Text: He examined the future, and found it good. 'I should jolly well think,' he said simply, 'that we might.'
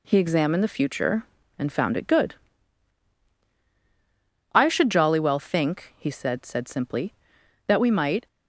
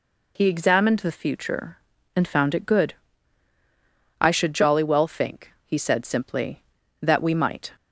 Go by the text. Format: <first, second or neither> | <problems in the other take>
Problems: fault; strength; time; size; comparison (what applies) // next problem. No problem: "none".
second | says "said" twice; at 6.4 s